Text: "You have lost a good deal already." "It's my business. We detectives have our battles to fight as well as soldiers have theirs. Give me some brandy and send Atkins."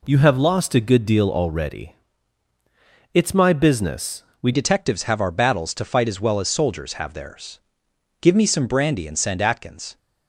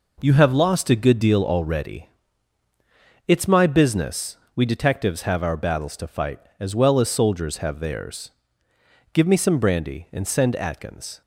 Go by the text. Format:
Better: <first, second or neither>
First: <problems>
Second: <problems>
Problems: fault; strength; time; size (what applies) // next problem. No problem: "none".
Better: second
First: changes voice at "detectives"; from 4.5 s on; 5.4 s long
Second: none